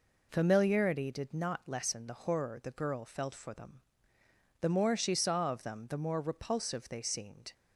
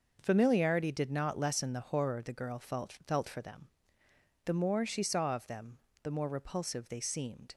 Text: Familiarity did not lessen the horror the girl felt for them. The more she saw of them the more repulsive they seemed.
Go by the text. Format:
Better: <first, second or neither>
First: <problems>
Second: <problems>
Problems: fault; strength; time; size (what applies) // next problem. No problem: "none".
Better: first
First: none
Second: says "felt" twice; at 3.0 s // pauses between "them" and "the"; slight; at 5.7 s; 0.24 s long